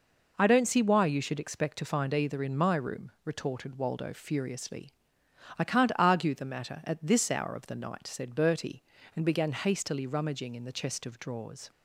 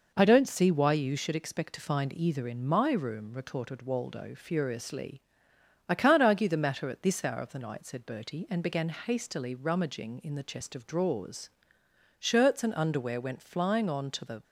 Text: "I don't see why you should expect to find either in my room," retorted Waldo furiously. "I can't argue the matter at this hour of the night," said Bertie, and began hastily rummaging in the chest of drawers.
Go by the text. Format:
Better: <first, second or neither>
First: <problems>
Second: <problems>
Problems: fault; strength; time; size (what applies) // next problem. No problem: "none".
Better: first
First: none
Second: goes on to say "Shirts and underwear went flying on to the"; strong; from 12.1 s on; 2.2 s long